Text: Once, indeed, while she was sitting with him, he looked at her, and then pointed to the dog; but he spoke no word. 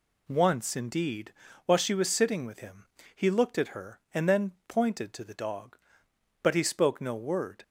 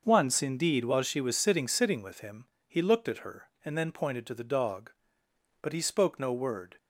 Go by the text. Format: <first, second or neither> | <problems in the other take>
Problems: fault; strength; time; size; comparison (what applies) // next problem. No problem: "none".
first | starts louder than the rest; noticeable; until 1.0 s; 6 dB // says "sitting" twice; at 1.6 s